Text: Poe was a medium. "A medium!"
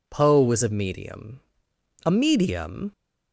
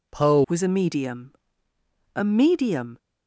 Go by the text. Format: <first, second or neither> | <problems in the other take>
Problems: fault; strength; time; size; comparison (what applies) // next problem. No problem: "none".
first | changes voice at "was"; from 0.4 s on; 2.5 s long